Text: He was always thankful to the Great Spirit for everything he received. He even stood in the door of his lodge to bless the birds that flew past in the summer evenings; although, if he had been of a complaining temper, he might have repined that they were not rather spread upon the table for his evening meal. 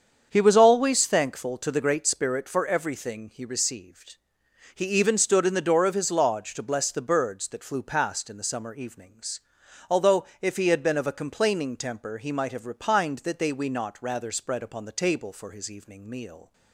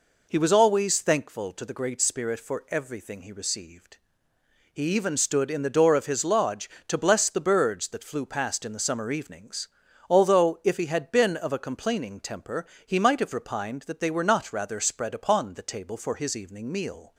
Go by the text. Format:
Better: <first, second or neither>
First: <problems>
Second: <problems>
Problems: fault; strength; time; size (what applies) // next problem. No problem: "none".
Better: second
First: starts louder than the rest; strong; until 1.3 s; 7.5 dB // says "we" for "were"; at 13.5 s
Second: none